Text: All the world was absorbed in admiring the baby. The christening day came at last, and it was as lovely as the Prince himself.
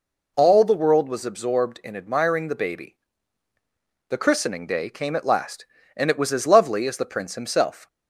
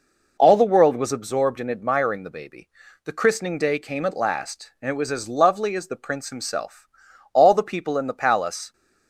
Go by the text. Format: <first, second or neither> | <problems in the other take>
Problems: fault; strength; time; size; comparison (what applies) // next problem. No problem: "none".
first | goes on to say "All the people in the palace"; from 7.3 s on; 1.4 s long